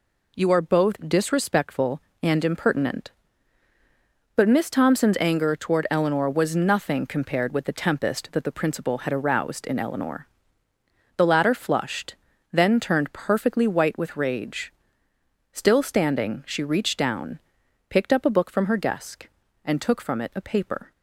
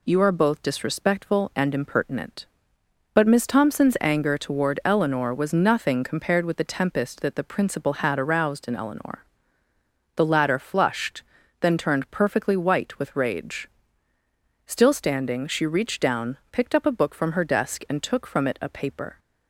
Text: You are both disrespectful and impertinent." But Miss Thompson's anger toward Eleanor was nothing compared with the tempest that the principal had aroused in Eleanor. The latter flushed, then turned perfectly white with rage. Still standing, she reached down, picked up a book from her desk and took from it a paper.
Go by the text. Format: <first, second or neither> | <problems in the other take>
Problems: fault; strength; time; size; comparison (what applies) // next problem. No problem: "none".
neither | none